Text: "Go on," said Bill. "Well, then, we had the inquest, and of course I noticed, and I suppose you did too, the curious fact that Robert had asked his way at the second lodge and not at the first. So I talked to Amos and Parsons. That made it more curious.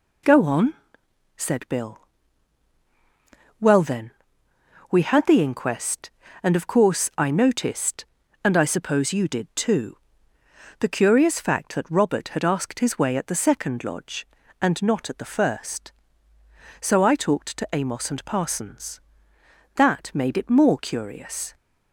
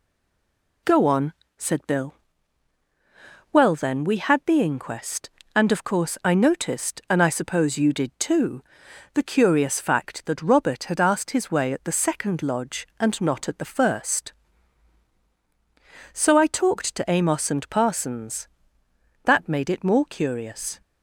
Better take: first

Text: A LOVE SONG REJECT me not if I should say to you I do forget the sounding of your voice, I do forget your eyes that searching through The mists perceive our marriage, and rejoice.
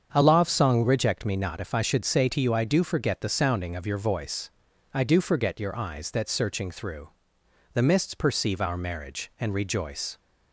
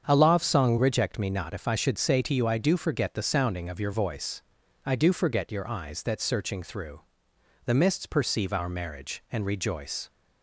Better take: neither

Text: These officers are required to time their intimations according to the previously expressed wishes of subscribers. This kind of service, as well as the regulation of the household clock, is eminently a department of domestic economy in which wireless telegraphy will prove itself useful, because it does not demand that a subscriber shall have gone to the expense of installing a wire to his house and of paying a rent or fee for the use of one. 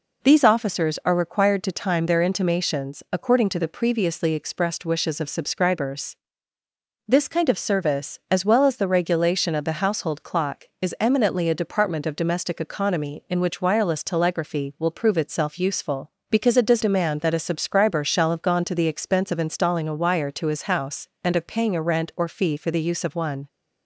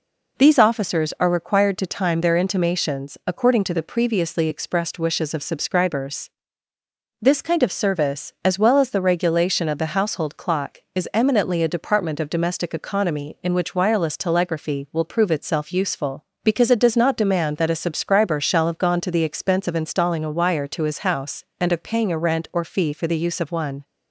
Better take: second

